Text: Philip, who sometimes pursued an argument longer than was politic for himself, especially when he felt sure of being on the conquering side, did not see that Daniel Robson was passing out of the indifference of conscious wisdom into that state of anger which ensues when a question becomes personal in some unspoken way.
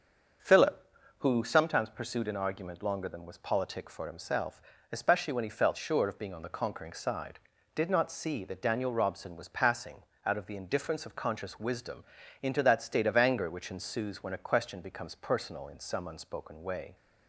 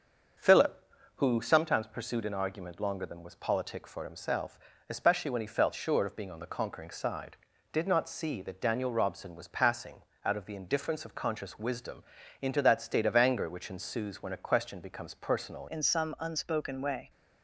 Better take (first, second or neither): first